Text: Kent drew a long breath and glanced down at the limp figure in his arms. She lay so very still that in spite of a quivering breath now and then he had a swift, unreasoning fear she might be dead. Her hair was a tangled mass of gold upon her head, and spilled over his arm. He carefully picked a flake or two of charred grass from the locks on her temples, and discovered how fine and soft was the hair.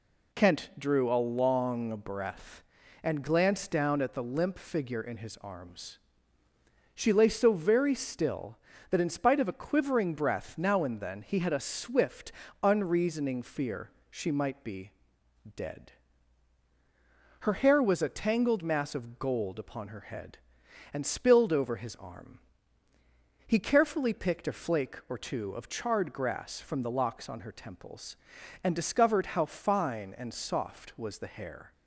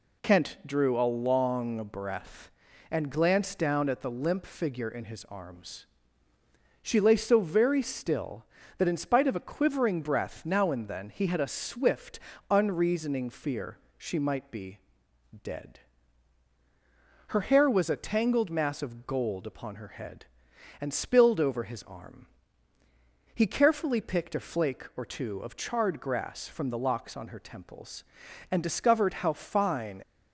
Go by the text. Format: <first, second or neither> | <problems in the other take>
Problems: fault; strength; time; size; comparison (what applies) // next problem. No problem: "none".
first | pauses between "fear" and "she"; slight; at 13.7 s; 0.20 s long; slight in the first // pauses between "be" and "dead"; noticeable; at 14.7 s; 0.66 s long; noticeable in the first // stops before "and soft was the hair"; at 30.0 s